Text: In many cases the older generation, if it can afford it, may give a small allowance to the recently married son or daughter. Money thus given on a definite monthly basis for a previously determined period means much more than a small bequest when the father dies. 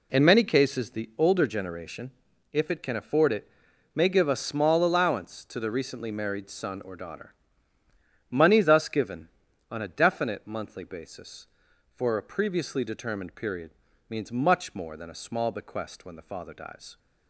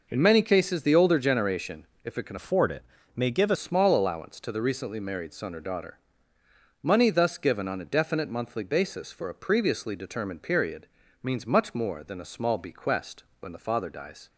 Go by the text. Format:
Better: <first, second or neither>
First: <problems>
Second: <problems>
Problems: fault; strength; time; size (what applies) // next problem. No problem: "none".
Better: first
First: pauses between "period" and "means"; at 13.7 s; 0.38 s long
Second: changes voice from "afford" to "a"; from 2.3 to 3.5 s; 1.2 s long // pauses between "period" and "means"; at 10.8 s; 0.38 s long // pauses between "bequest" and "when"; slight; at 13.2 s; 0.16 s long